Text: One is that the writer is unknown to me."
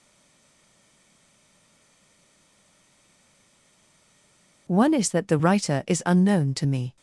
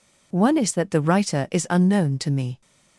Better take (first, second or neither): second